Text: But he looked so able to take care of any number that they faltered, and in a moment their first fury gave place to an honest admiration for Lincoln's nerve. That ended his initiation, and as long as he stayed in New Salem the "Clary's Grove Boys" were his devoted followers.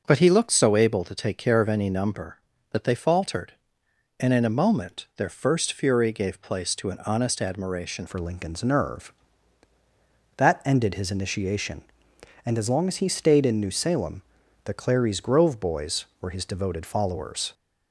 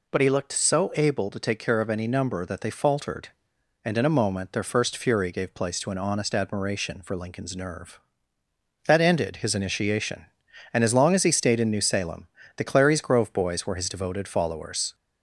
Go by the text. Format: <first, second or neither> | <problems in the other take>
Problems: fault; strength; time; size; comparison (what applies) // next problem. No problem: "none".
second | changes voice at "for"; from 8.0 s on; 9.5 s long // pauses between "Salem" and "the"; at 14.2 s; 0.42 s long; slight in the second